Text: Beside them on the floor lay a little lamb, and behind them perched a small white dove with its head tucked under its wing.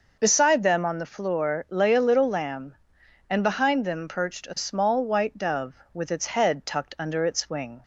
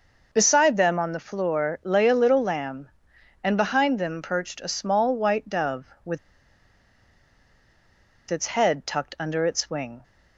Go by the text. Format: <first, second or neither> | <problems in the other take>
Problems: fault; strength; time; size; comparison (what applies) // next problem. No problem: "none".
first | pauses between "with" and "its"; strong; at 6.1 s; 2.1 s long